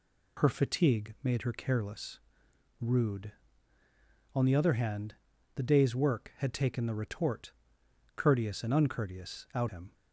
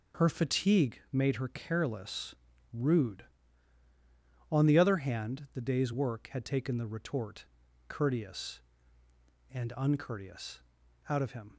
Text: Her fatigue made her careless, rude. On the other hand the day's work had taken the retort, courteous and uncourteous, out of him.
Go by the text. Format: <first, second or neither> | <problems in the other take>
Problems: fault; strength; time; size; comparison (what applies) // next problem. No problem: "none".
second | pauses between "hand" and "the"; at 5.1 s; 0.40 s long // skips "of"; at 9.6 s